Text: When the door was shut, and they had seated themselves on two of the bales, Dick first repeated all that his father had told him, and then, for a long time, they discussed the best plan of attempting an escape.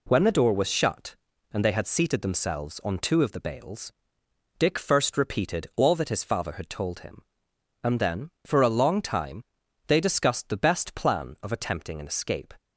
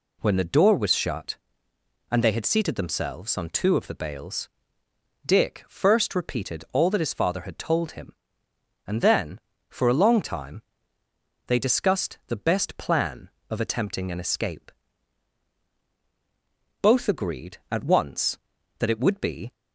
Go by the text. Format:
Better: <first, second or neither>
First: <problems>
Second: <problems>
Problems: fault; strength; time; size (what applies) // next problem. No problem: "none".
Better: first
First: none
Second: goes on to say "Both agreed at once that it would be"; strong; from 16.8 s on; 2.7 s long